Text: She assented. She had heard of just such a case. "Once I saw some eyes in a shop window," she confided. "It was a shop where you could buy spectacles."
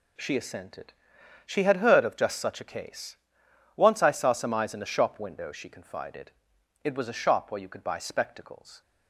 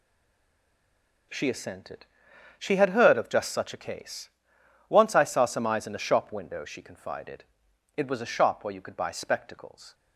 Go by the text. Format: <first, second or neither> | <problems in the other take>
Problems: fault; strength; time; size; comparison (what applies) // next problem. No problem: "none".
first | stays silent before the first word; noticeable; until 1.2 s; 1.2 s long